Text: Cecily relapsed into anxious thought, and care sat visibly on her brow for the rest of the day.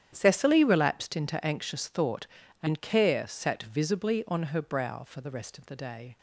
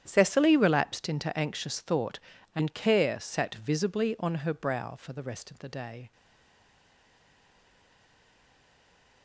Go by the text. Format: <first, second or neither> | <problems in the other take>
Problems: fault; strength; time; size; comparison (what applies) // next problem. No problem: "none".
first | starts louder than the rest; strong; until 1.0 s; 10 dB; strong in the first // stays silent after the last word; strong; from 6.1 s on; 3.1 s long